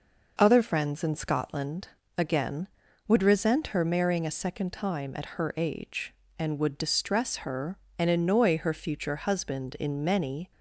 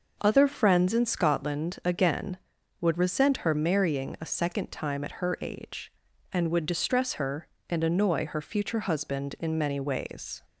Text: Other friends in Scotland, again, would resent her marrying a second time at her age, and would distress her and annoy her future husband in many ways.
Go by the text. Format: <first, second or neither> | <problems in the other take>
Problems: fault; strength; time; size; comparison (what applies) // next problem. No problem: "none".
second | stops before "ways"; at 10.5 s